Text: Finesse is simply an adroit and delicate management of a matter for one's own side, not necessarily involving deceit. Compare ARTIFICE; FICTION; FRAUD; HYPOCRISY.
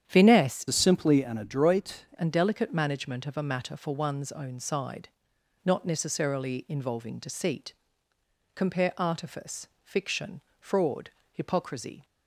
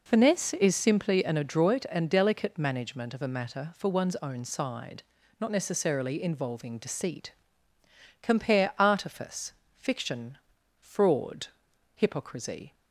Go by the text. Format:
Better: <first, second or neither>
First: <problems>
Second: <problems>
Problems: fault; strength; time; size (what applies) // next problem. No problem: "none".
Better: second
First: starts louder than the rest; strong; until 1.0 s; 9 dB // changes voice from "is" to "adroit"; from 0.6 to 2.0 s; 1.4 s long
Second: none